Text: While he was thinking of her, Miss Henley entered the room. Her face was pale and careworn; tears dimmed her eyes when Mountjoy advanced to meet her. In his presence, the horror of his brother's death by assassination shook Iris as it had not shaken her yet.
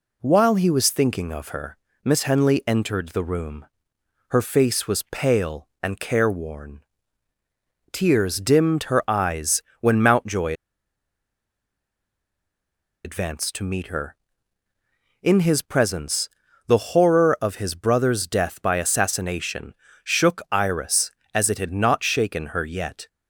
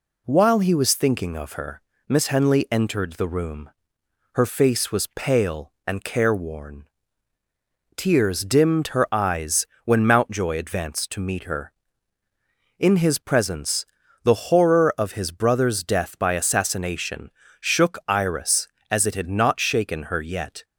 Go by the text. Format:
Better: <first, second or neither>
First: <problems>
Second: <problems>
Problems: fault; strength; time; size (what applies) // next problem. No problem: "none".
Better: second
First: pauses between "eyes" and "when"; slight; at 9.6 s; 0.18 s long // pauses between "Mountjoy" and "advanced"; strong; at 10.5 s; 2.5 s long // pauses between "assassination" and "shook"; slight; at 19.7 s; 0.30 s long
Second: pauses between "eyes" and "when"; slight; at 9.6 s; 0.18 s long // pauses between "assassination" and "shook"; slight; at 17.3 s; 0.30 s long